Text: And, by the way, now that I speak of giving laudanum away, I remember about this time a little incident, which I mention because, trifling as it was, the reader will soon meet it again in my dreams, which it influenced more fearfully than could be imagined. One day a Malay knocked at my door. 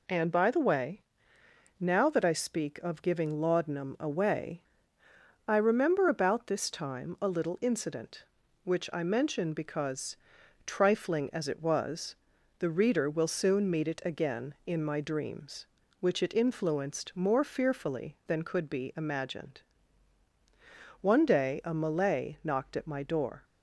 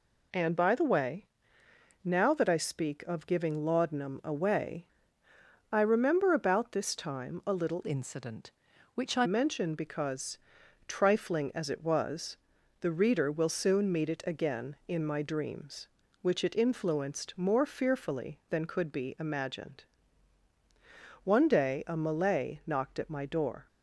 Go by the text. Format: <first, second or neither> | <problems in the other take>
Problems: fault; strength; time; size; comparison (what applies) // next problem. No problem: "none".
first | changes voice from "incident" to "I"; from 7.8 to 9.2 s; 1.4 s long